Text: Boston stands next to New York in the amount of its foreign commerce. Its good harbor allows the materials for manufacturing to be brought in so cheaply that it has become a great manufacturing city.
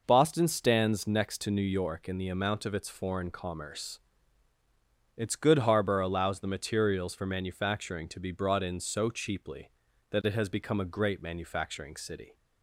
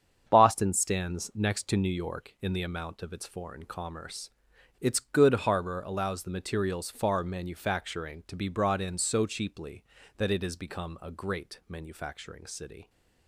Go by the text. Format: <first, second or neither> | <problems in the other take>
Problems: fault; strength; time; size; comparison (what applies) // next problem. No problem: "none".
first | starts louder than the rest; strong; until 1.2 s; 7.5 dB // says "far" for "for"; at 6.9 s